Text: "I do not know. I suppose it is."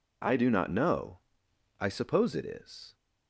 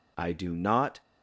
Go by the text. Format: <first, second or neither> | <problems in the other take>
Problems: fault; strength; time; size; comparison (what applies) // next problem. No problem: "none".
first | stops before "know I suppose it is"; at 1.0 s